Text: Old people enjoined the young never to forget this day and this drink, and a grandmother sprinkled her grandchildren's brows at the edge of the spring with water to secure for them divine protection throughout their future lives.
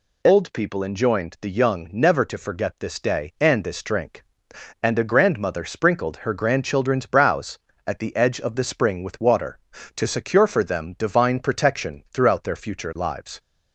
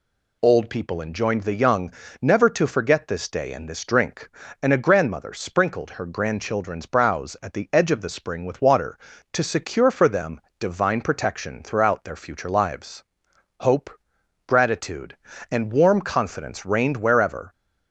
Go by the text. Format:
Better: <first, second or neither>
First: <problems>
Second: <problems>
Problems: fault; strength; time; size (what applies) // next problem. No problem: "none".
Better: first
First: none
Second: pauses between "young" and "never"; slight; at 1.9 s; 0.30 s long // pauses between "them" and "divine"; slight; at 10.3 s; 0.22 s long // goes on to say "Hope gratitude and warm confidence reigned wherever"; strong; from 13.5 s on; 3.9 s long